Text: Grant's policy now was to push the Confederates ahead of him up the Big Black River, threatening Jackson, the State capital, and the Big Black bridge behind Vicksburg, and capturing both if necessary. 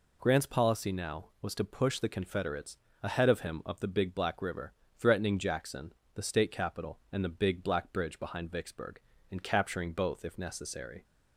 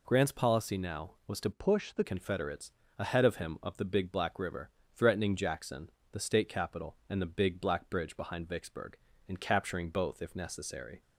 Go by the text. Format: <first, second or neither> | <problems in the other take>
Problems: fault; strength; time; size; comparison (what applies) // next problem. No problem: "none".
first | changes voice from "push" to "the"; from 1.5 to 2.0 s; 0.5 s long // pauses between "Confederates" and "ahead"; slight; at 2.7 s; 0.28 s long; slight in the first